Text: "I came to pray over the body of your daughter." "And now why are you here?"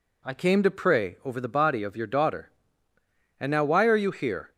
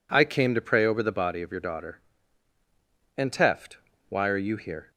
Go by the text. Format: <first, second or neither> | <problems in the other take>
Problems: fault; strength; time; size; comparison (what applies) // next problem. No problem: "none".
first | says "teft" for "now"; at 3.3 s